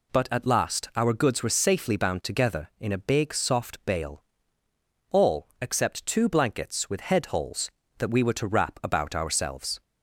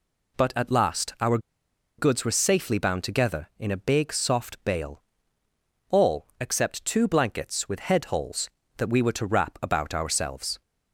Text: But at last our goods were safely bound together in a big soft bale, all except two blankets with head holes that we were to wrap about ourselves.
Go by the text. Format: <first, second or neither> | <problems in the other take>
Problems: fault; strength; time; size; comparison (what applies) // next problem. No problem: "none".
first | pauses between "our" and "goods"; noticeable; at 1.3 s; 0.60 s long